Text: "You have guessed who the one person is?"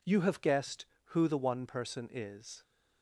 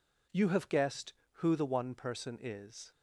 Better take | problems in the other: neither | none

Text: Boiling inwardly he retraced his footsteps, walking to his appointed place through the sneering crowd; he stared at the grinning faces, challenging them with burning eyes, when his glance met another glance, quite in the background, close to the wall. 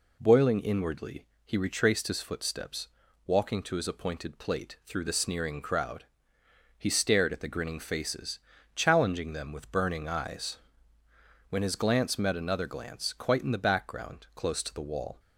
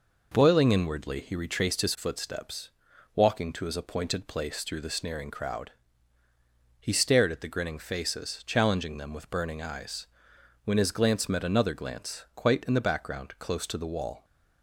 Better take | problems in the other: second | pauses between "inwardly" and "he"; slight; at 1.2 s; 0.22 s long // says "plate" for "place"; at 4.3 s

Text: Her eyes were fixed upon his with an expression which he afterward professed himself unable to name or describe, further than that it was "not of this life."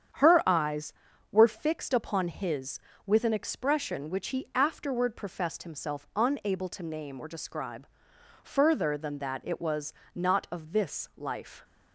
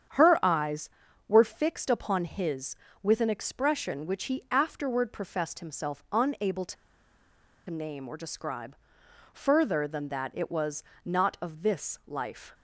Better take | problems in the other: first | starts louder than the rest; strong; until 1.5 s; 8.5 dB; strong in the first // pauses between "to" and "name"; noticeable; at 6.7 s; 0.94 s long // pauses between "was" and "not"; slight; at 10.8 s; 0.22 s long; slight in the first

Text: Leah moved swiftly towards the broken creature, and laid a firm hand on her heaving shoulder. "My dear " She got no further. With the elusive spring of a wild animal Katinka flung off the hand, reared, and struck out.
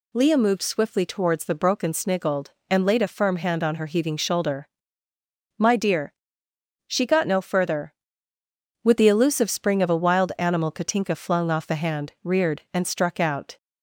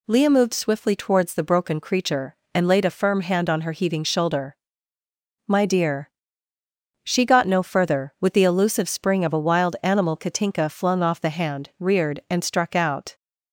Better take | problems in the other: second | says "sniggled" for "creature"; at 1.9 s

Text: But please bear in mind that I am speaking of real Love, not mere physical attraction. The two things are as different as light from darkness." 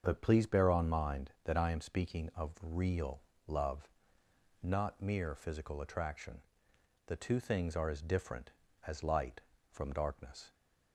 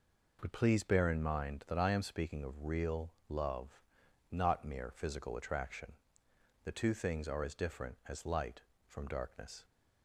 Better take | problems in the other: second | starts louder than the rest; until 1.0 s; 7 dB // says "on" for "in"; at 0.6 s // pauses between "real" and "Love"; slight; at 3.2 s; 0.26 s long; slight in the second

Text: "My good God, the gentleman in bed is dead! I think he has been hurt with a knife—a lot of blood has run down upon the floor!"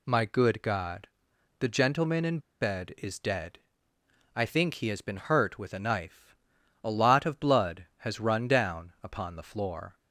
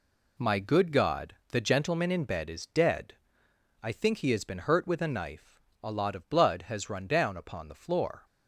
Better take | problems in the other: second | pauses between "in" and "bed"; slight; at 2.3 s; 0.21 s long

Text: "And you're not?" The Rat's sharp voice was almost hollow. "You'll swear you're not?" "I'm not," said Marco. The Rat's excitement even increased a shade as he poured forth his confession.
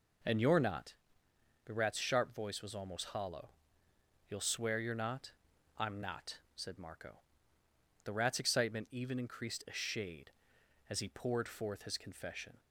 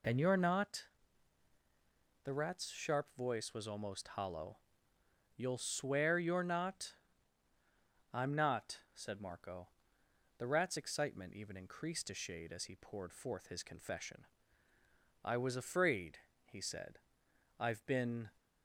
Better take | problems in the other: first | goes on to say "I was afraid he said I've been"; strong; from 15.2 s on; 3.0 s long

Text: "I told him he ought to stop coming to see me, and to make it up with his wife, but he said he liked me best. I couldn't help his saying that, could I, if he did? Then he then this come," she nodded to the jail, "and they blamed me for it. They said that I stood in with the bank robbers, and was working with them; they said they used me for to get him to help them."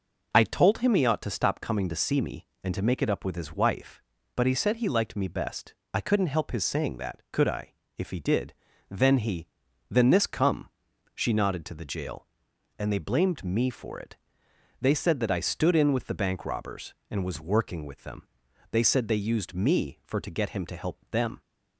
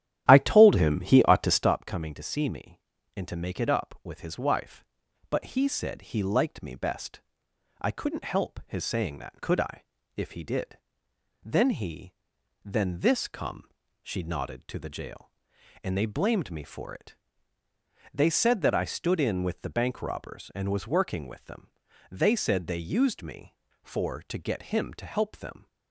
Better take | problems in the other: first | starts louder than the rest; strong; until 1.8 s; 11.5 dB // pauses between "he" and "then"; noticeable; at 12.1 s; 0.56 s long; also in the first

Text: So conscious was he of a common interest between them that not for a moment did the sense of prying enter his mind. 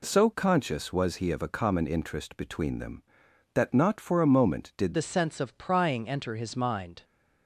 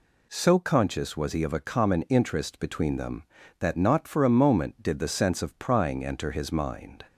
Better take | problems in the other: second | changes voice at "the"; from 4.9 s on; 2.1 s long

